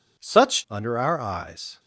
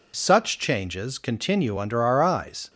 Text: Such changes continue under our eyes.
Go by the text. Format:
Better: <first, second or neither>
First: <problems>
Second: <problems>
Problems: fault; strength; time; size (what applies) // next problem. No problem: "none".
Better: second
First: skips "changes continue"; at 0.6 s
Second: none